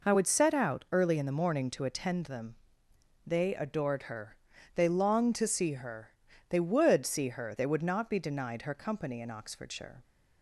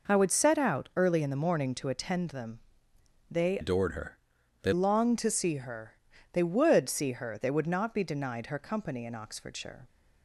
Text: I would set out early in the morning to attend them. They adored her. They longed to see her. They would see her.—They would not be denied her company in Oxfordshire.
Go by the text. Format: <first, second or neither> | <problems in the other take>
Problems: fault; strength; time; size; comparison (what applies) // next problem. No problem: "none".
first | changes voice from "adored" to "They"; from 3.6 to 4.7 s; 1.1 s long